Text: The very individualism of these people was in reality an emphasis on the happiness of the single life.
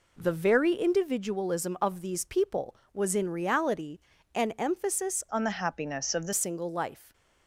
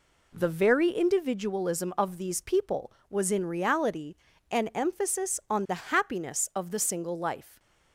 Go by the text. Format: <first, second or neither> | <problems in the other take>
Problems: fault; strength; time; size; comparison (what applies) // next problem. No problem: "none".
second | pauses between "reality" and "an"; slight; at 3.9 s; 0.34 s long; slight in the second // changes voice from "on" to "the"; from 5.2 to 6.3 s; 1.1 s long